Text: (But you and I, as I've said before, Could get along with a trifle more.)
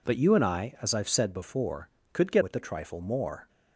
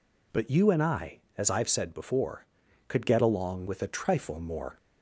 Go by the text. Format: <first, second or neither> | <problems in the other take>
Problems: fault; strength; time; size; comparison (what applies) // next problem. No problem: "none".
second | skips "along"; at 2.4 s